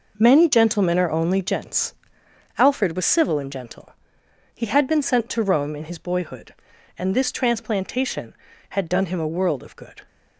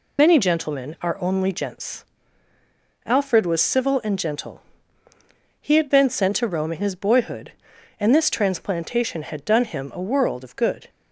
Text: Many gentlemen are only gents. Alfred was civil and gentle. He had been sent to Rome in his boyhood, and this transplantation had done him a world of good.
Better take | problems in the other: first | loses the start of "Many"; at 0.1 s; 60 ms

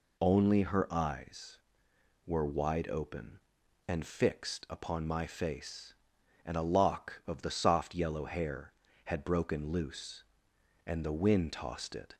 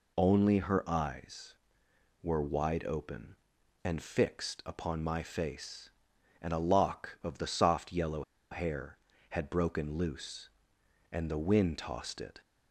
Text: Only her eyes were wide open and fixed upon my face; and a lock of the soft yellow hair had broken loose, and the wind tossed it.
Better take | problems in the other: first | pauses between "yellow" and "hair"; slight; at 8.2 s; 0.29 s long

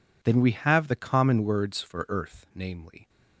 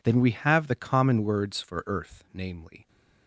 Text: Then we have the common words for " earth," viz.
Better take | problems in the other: neither | none

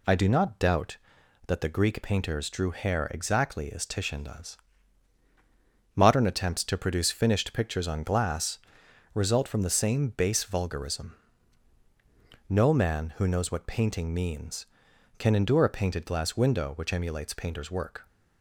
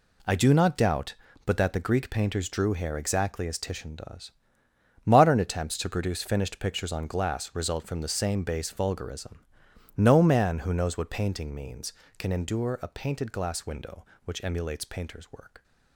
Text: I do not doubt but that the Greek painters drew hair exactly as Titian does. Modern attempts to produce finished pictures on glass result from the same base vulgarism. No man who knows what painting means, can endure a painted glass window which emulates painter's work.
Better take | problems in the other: second | skips "but"; at 1.2 s // pauses between "glass" and "result"; noticeable; at 8.5 s; 0.56 s long

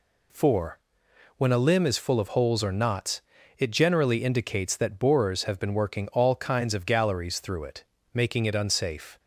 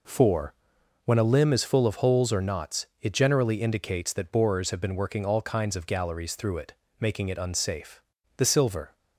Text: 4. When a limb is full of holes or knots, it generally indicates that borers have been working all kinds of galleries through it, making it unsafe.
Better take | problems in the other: first | goes on to say "The silver"; from 8.3 s on; 0.60 s long

